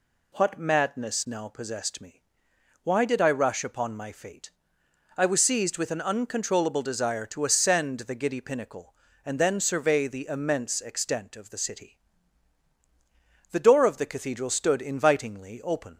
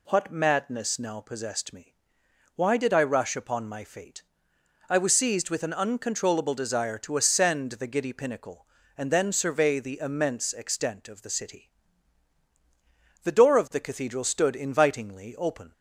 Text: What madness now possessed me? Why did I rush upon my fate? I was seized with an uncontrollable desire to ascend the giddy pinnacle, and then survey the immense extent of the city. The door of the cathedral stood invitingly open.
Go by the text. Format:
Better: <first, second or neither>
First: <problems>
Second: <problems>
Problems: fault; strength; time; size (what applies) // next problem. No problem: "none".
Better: neither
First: none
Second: none